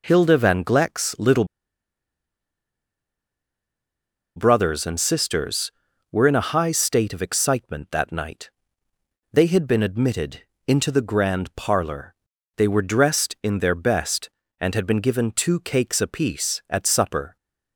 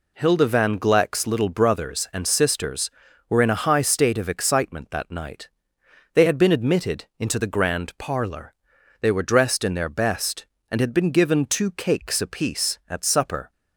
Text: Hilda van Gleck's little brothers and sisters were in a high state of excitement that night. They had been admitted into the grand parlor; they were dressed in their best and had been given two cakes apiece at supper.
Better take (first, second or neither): second